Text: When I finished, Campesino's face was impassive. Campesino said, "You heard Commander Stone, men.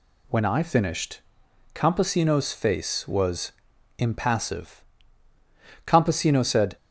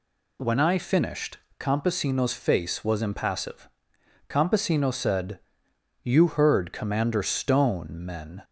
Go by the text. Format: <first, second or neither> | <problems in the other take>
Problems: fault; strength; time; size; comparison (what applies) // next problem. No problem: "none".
second | pauses between "was" and "impassive"; noticeable; at 3.5 s; 0.46 s long // stops before "You heard Commander Stone men"; at 6.7 s